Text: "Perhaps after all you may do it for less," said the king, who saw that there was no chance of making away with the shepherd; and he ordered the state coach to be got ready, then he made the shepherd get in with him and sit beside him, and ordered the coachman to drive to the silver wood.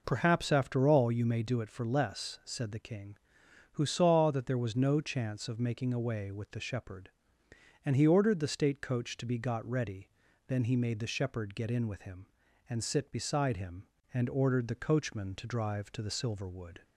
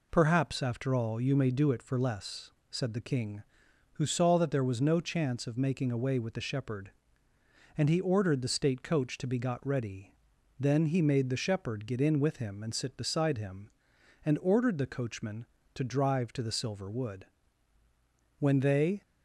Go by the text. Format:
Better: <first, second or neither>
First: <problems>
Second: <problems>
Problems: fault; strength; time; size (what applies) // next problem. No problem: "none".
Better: first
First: none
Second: goes on to say "When they"; noticeable; from 18.3 s on; 0.62 s long